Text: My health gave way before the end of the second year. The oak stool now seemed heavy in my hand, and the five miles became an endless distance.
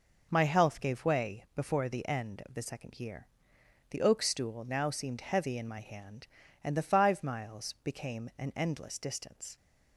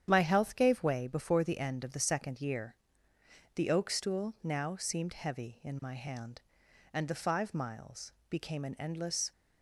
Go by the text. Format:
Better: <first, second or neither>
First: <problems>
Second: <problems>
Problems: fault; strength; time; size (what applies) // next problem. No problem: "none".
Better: first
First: none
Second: starts louder than the rest; strong; until 1.0 s; 9 dB // pauses between "miles" and "became"; slight; at 8.1 s; 0.16 s long // stops before "distance"; at 9.3 s